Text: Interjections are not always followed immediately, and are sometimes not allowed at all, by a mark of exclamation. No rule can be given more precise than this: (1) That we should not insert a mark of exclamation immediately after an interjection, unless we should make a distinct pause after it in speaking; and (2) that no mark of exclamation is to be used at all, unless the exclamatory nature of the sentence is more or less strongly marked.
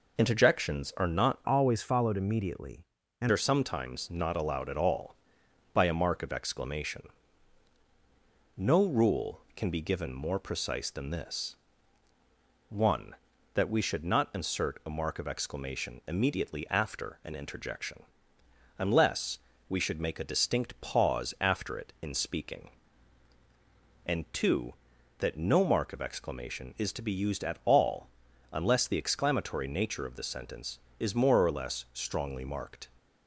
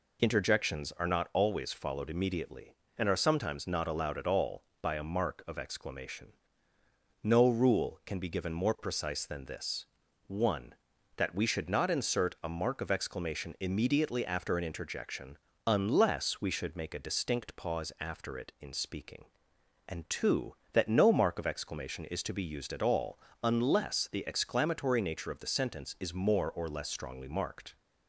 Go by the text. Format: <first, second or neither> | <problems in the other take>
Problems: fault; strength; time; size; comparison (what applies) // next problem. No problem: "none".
second | changes voice from "always" to "and"; from 1.4 to 3.2 s; 1.8 s long // pauses between "unless" and "we"; slight; at 19.3 s; 0.32 s long